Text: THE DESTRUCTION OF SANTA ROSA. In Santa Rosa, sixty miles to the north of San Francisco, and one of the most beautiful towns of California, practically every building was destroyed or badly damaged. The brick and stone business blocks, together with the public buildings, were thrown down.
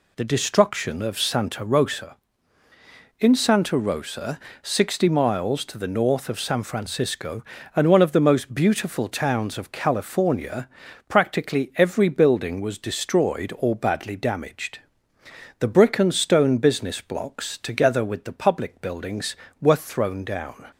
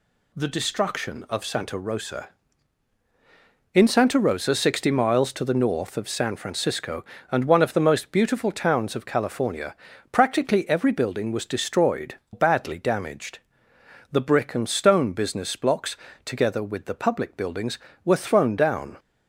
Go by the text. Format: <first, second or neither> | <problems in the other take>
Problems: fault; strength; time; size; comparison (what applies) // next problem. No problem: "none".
first | skips "or"; at 12.2 s